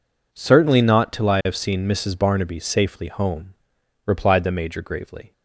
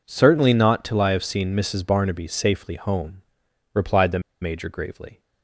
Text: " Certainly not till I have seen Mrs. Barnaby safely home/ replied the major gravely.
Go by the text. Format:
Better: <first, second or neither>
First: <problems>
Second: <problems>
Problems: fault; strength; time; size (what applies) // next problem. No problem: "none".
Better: first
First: none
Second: pauses between "the" and "major"; slight; at 4.1 s; 0.21 s long